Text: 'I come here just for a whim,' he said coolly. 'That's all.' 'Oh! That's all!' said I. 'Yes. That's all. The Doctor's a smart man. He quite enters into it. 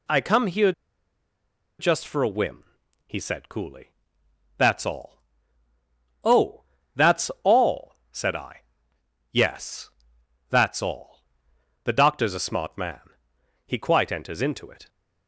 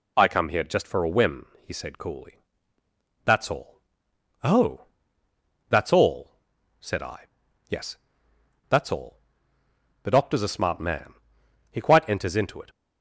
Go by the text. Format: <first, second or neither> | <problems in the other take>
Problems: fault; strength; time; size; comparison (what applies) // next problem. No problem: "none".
second | pauses between "here" and "just"; at 0.7 s; 1.0 s long